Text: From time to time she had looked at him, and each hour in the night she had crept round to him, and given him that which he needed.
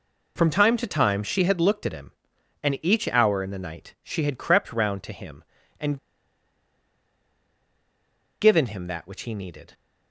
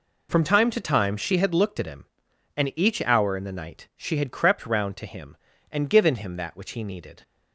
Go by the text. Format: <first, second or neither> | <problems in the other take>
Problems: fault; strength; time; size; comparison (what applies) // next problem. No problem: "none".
second | pauses between "and" and "given"; strong; at 5.9 s; 2.4 s long